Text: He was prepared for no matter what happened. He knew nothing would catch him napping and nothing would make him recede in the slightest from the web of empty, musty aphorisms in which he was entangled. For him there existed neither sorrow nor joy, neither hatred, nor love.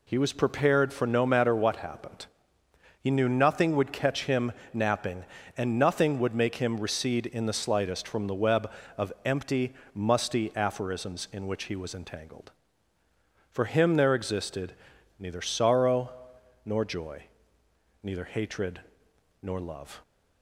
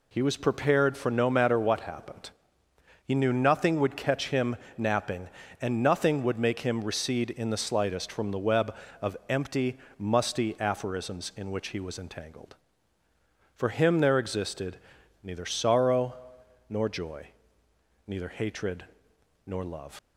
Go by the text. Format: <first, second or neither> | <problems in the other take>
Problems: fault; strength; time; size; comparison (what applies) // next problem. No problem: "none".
first | pauses between "him" and "napping"; slight; at 4.5 s; 0.20 s long; slight in the first // pauses between "existed" and "neither"; noticeable; at 14.7 s; 0.48 s long; noticeable in the first // pauses between "sorrow" and "nor"; noticeable; at 16.1 s; 0.56 s long; noticeable in the first // leaves "love" unfinished; at 19.9 s; 70 ms